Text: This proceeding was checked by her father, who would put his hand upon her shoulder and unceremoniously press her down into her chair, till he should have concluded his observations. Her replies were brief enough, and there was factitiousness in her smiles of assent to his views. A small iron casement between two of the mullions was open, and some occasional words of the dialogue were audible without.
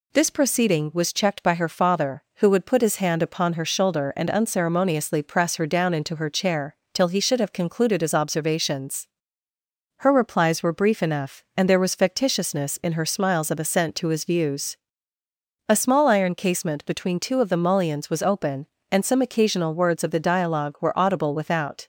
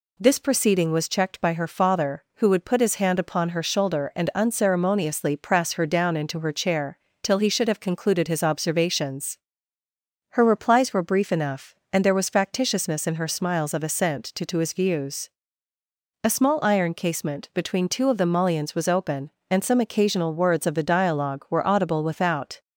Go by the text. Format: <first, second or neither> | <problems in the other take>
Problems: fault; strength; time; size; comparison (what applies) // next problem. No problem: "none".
first | says "to" twice; at 14.4 s